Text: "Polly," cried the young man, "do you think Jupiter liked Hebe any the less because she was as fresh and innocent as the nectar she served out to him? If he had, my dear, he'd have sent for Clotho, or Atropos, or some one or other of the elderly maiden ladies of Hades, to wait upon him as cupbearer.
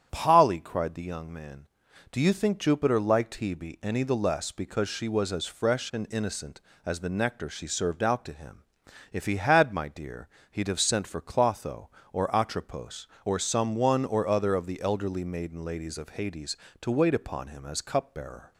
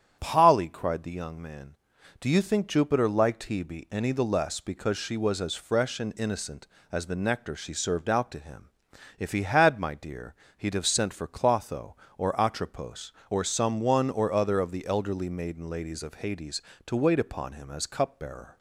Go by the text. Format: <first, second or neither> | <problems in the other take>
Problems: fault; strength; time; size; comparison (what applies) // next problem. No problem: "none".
neither | starts louder than the rest; strong; the same in both